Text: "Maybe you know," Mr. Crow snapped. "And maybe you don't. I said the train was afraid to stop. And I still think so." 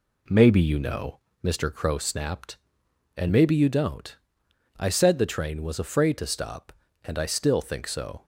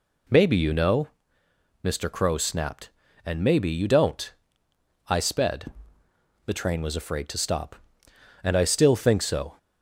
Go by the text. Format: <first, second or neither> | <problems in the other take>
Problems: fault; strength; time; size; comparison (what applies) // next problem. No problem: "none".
first | says "sped" for "said"; at 5.1 s